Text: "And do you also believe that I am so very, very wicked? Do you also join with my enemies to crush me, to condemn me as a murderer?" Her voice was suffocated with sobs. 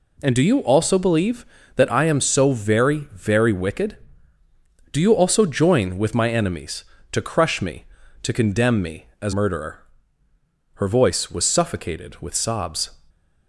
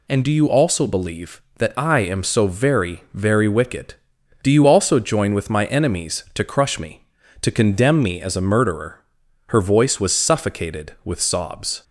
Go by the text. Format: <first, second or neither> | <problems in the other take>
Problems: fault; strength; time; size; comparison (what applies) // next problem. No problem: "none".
second | skips "a"; at 9.3 s